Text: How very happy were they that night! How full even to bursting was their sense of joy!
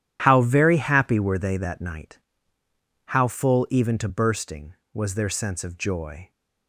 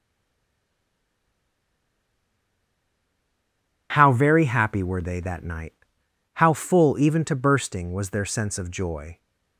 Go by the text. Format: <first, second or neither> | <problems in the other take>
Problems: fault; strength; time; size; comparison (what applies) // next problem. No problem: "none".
first | stays silent before the first word; strong; until 3.9 s; 3.9 s long